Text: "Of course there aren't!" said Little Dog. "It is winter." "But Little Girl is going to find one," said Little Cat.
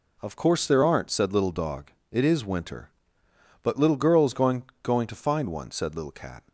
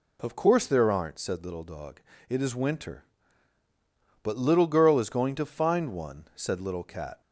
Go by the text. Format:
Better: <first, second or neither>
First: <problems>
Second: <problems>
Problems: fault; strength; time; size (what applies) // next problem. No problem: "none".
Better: second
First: says "going" twice; at 4.8 s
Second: none